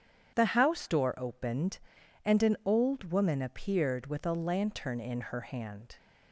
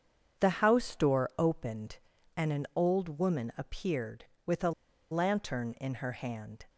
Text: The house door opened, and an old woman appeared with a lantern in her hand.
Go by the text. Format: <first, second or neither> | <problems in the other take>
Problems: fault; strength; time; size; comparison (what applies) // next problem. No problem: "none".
first | starts louder than the rest; strong; until 1.4 s; 7.5 dB; strong in the first // pauses between "a" and "lantern"; at 4.7 s; 0.40 s long